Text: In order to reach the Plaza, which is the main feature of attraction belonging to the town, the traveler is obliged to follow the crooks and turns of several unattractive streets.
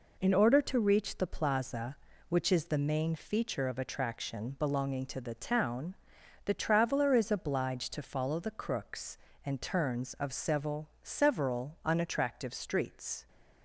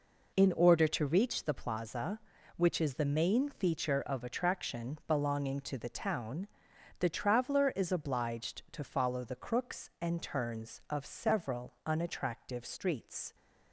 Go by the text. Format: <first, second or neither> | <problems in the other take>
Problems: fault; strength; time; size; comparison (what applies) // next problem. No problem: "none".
second | says "several" twice; at 11.0 s